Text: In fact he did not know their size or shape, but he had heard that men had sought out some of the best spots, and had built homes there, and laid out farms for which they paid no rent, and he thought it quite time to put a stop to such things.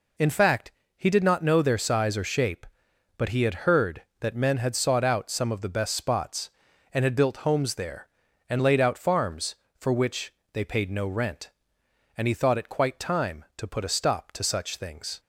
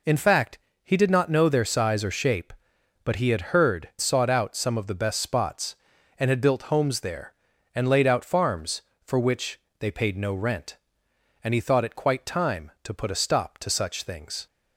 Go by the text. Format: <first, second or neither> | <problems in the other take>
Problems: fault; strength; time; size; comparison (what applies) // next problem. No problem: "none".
first | pauses between "fact" and "he"; slight; at 0.5 s; 0.26 s long; slight in the first // skips "that men had"; at 3.9 s // pauses between "which" and "they"; slight; at 9.5 s; 0.22 s long; slight in the first